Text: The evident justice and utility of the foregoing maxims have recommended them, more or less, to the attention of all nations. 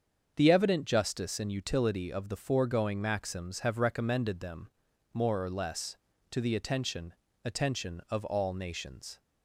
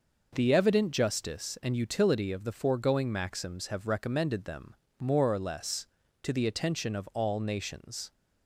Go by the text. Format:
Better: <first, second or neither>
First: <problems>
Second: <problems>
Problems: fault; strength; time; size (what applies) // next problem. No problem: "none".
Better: second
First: starts louder than the rest; until 1.3 s; 7 dB // says "attention" twice; at 7.4 s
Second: none